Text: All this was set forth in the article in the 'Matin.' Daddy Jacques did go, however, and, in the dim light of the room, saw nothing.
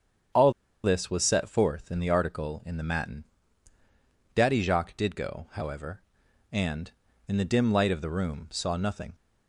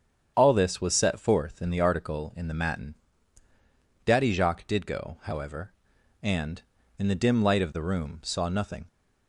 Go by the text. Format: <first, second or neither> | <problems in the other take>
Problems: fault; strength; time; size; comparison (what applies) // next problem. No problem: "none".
second | starts louder than the rest; strong; until 1.6 s; 8 dB; strong in the second // pauses between "All" and "this"; slight; at 0.5 s; 0.33 s long